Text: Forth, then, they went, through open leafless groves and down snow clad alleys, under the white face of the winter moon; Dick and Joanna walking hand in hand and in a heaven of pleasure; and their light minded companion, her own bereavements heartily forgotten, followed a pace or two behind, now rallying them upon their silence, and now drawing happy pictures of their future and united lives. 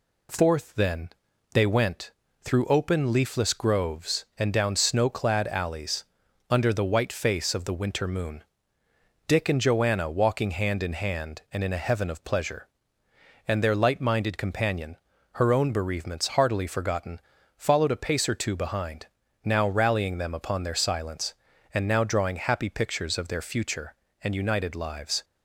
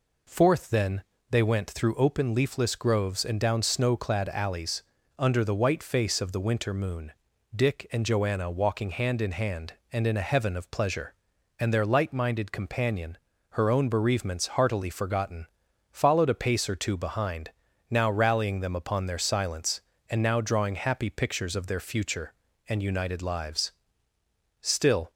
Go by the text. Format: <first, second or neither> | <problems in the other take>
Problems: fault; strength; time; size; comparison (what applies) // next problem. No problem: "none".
first | goes on to say "Still"; from 24.5 s on; 0.50 s long